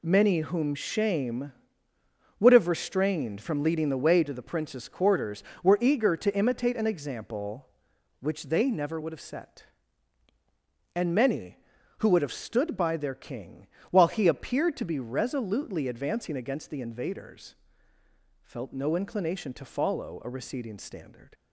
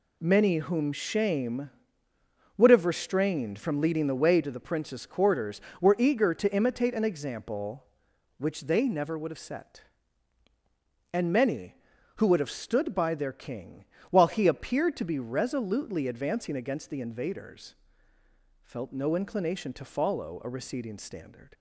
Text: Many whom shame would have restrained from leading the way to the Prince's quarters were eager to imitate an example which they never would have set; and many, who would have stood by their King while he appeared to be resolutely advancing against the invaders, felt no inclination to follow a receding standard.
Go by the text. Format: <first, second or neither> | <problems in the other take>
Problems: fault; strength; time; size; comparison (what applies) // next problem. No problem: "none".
neither | pauses between "King" and "while"; slight; the same in both